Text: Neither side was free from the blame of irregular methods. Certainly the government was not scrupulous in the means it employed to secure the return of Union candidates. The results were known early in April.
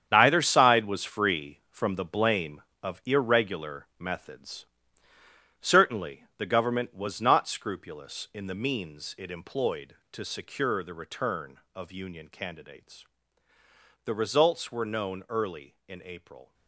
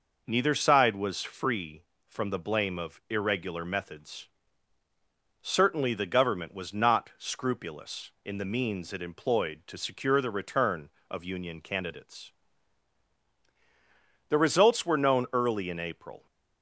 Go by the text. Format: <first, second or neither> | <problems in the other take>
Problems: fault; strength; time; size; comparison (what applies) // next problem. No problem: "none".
second | gets quieter; strong; throughout; 11 dB